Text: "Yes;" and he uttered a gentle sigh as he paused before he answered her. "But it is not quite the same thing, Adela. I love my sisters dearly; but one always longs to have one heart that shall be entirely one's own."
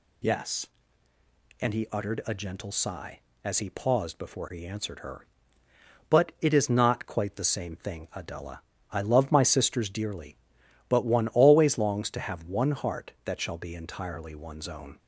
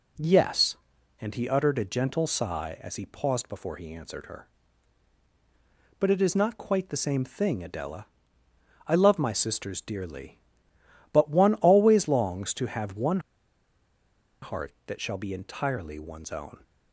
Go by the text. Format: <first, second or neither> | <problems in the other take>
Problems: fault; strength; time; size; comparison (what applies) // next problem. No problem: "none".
first | pauses between "one" and "heart"; at 13.1 s; 1.2 s long